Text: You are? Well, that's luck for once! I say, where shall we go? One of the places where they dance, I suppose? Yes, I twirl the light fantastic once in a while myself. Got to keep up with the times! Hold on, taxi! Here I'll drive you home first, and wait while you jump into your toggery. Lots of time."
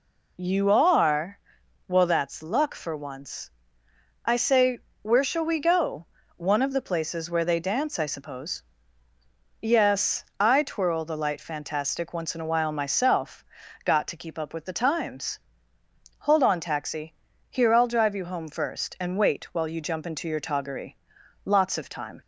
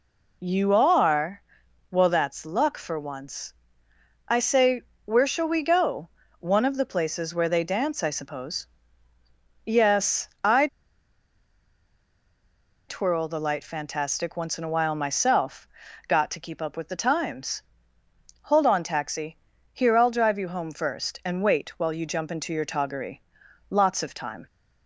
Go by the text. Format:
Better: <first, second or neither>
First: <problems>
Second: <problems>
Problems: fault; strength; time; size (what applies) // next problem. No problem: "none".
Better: first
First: none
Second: pauses between "I" and "twirl"; strong; at 10.6 s; 2.2 s long